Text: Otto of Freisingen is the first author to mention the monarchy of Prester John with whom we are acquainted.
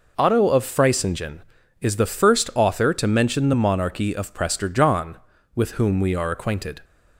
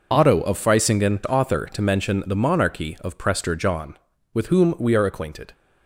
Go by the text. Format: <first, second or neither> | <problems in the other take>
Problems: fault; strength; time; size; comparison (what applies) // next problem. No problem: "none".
first | skips "is the first"; at 1.2 s